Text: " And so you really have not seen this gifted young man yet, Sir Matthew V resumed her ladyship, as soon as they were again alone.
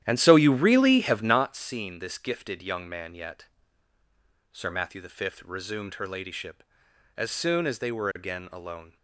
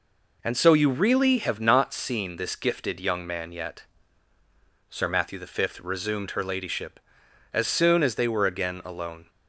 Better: second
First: starts louder than the rest; strong; until 1.4 s; 11.5 dB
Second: none

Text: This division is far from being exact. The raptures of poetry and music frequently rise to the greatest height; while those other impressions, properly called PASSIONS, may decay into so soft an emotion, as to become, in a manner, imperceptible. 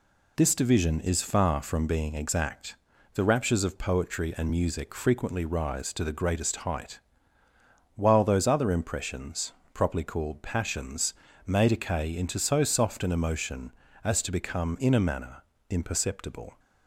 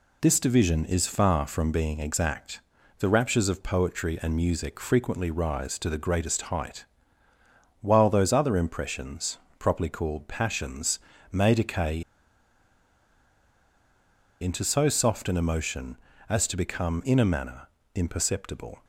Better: first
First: none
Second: pauses between "decay" and "into"; strong; at 12.0 s; 2.3 s long

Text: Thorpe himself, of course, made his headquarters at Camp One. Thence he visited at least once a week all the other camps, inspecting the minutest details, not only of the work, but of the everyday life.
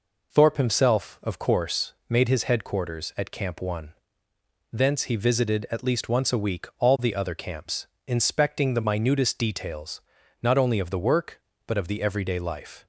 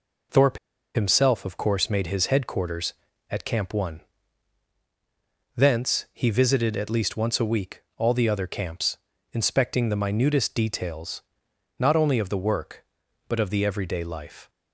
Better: first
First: none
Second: pauses between "Thorpe" and "himself"; at 0.5 s; 0.36 s long

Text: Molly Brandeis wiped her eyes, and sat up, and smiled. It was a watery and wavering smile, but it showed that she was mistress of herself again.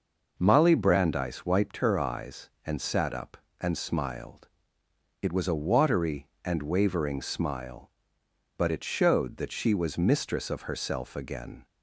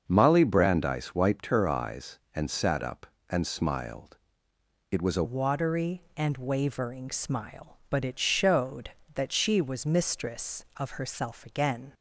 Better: first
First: none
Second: starts louder than the rest; until 1.0 s; 6.5 dB // changes voice at "watery"; from 5.2 s on; 6.7 s long

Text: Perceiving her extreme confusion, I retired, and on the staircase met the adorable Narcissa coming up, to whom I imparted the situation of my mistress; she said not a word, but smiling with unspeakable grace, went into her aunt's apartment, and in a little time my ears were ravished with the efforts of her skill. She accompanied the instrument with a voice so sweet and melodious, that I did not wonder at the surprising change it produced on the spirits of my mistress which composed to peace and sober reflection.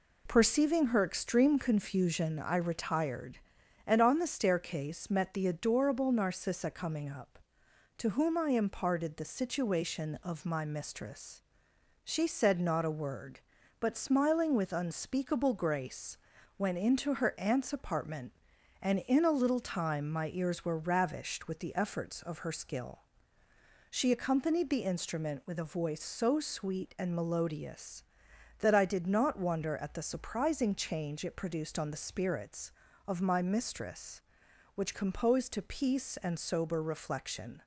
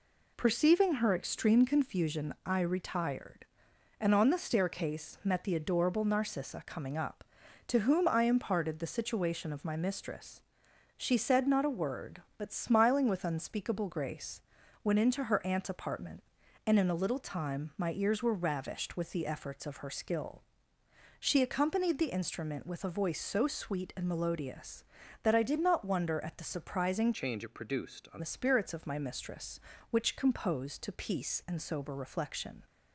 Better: first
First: none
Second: changes voice from "change" to "on"; from 27.1 to 28.2 s; 1.1 s long

